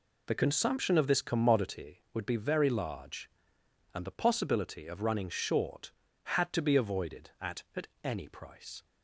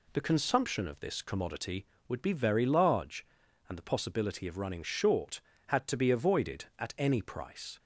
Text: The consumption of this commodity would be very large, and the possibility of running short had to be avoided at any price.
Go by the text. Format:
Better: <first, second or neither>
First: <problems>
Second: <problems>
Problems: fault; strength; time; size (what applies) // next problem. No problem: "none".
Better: second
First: says "at" twice; at 7.7 s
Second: none